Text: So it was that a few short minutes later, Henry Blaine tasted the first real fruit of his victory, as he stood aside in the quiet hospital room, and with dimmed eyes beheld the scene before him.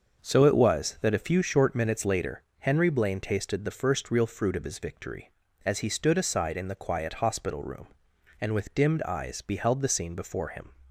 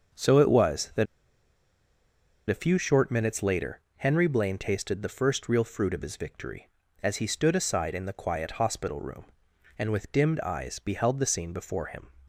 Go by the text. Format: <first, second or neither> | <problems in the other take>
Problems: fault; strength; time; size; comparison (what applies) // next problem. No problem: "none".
first | starts louder than the rest; until 2.6 s; 6 dB; noticeable in the first // pauses between "that" and "a"; strong; at 1.0 s; 1.4 s long